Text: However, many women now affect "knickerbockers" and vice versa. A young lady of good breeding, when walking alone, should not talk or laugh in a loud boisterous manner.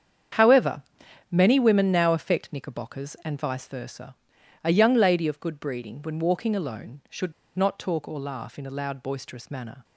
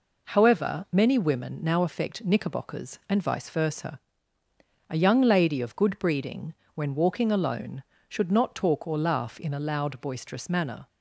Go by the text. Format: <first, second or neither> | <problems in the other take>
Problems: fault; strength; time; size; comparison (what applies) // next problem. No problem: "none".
second | starts louder than the rest; strong; until 1.8 s; 8 dB // pauses between "should" and "not"; slight; at 7.3 s; 0.24 s long